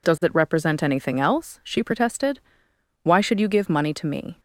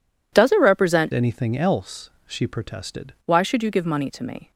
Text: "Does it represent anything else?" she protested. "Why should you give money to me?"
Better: first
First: none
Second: changes voice from "anything" to "protested"; from 1.1 to 3.1 s; 2.0 s long

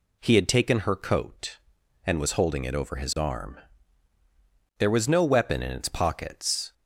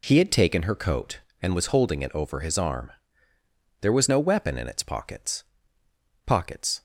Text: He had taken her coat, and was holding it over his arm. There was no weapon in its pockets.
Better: first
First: none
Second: says "pockets" twice; at 6.2 s

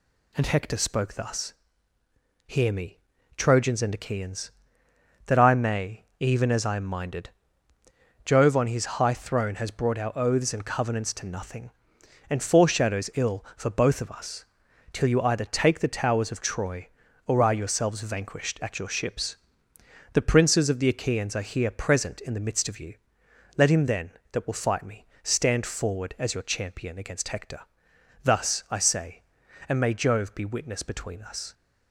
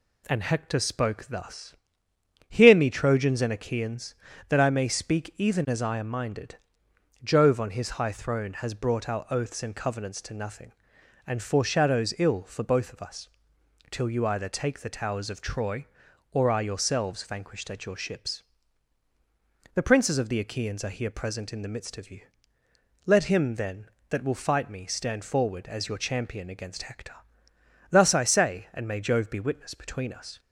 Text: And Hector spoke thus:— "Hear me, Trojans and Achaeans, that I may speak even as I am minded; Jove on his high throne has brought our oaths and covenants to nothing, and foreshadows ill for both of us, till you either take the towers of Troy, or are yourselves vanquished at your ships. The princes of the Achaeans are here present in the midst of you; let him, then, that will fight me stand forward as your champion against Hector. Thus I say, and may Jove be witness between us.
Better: second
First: skips "speak"; at 6.1 s // pauses between "me" and "stand"; slight; at 25.0 s; 0.18 s long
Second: none

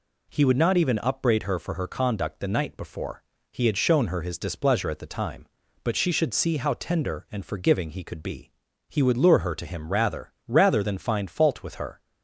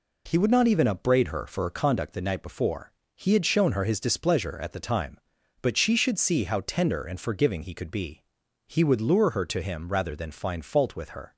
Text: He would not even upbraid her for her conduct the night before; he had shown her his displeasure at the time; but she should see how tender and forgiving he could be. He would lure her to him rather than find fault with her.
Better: second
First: says "rather" twice; at 10.4 s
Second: none

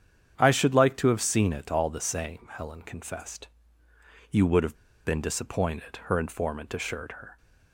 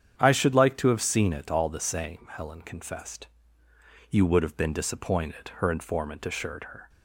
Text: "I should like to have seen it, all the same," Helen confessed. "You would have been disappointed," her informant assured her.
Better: second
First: starts louder than the rest; strong; until 1.3 s; 8 dB // pauses between "have" and "been"; slight; at 4.7 s; 0.28 s long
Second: starts louder than the rest; strong; until 1.2 s; 8 dB

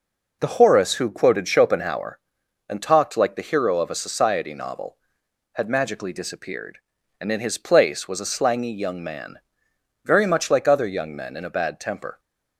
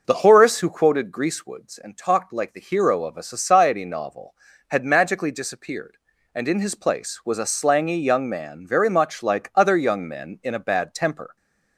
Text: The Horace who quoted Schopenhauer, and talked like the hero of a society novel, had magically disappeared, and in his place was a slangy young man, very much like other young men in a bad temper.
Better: first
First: none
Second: says "Greasewoods" for "Schopenhauer"; at 1.0 s

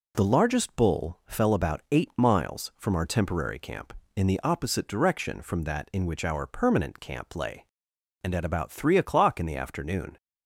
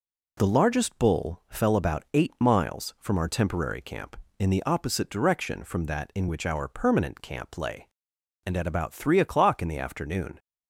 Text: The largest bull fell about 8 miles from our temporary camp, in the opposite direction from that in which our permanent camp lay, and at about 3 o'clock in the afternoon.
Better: neither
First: none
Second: none

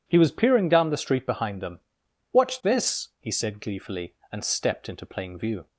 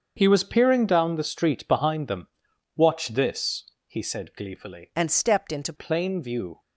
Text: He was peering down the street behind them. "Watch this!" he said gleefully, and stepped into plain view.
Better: first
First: none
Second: starts louder than the rest; until 1.1 s; 7 dB // changes voice from "and" to "into"; from 4.9 to 5.7 s; 0.8 s long

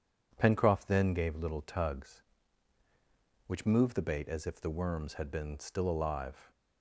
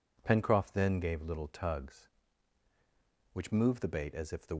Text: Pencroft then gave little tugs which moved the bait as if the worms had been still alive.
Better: first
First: none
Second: stops before "worms had been still alive"; at 4.5 s

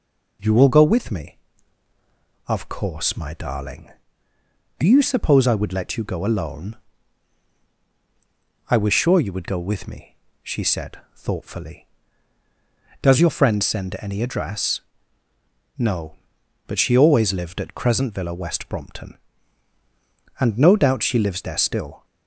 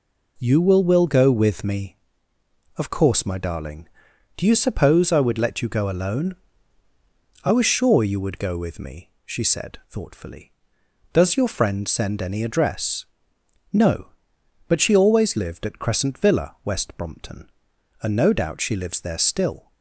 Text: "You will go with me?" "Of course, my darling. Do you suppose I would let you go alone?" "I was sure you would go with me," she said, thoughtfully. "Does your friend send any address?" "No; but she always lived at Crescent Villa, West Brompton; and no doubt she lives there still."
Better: first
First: none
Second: says "will" twice; at 0.8 s

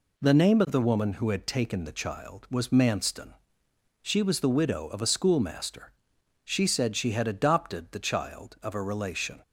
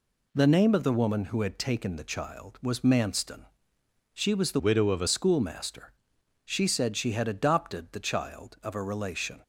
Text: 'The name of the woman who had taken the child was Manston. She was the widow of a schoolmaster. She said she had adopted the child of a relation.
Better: first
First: none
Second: changes voice from "widow" to "a"; from 4.5 to 5.0 s; 0.5 s long

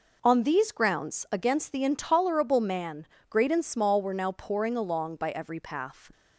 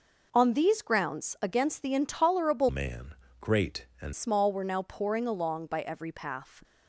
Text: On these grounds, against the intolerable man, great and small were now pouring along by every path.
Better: first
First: none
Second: changes voice from "man" to "and"; from 2.6 to 4.1 s; 1.5 s long

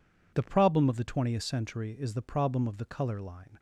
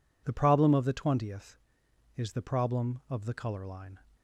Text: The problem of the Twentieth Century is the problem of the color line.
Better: first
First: none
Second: skips "Century"; at 1.8 s

